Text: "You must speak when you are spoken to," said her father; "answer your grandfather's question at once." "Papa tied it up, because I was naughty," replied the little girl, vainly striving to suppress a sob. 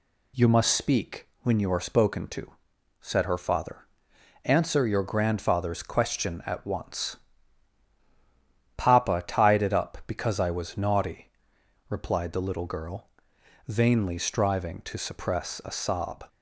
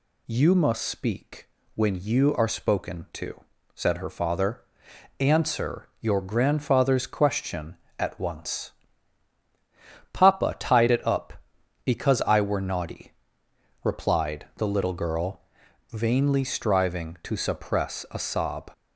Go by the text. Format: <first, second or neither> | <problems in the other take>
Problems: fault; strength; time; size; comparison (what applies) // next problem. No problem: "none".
first | pauses between "speak" and "when"; slight; at 1.4 s; 0.26 s long // says "were" for "was"; at 12.3 s